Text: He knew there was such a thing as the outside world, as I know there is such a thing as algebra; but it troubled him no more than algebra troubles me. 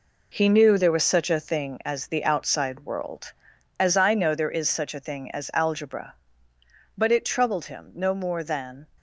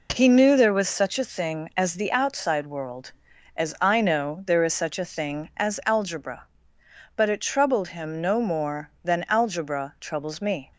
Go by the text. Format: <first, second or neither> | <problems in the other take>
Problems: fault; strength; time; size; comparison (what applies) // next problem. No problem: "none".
second | stops before "algebra troubles me"; at 8.9 s